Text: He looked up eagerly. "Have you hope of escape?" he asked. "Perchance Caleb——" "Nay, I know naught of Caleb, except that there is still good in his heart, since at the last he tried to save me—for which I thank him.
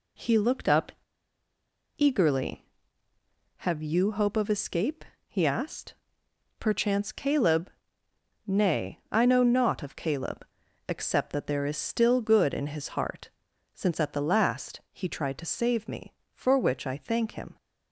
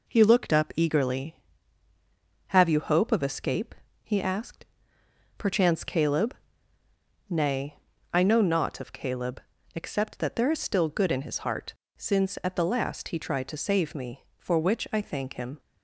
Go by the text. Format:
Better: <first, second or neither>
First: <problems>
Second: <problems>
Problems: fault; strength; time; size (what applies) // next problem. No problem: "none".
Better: second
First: pauses between "up" and "eagerly"; at 0.9 s; 1.0 s long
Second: none